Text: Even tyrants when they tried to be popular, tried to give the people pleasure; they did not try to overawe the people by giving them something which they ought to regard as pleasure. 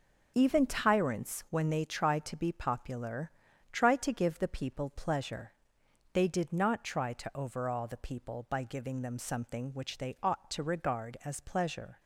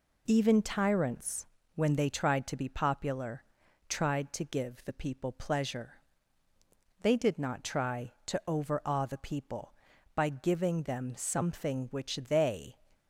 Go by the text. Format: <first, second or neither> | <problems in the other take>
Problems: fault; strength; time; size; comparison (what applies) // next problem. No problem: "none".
first | pauses between "tyrants" and "when"; slight; at 1.4 s; 0.30 s long // stops before "ought to regard as pleasure"; at 12.9 s